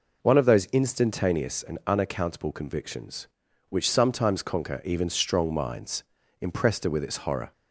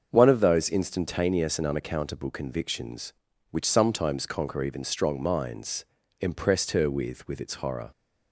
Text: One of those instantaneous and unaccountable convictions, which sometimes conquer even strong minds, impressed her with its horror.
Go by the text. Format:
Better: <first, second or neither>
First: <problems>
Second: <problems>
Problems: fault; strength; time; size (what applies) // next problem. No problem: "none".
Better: first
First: none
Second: starts louder than the rest; until 1.1 s; 6.5 dB // says "with" twice; at 7.2 s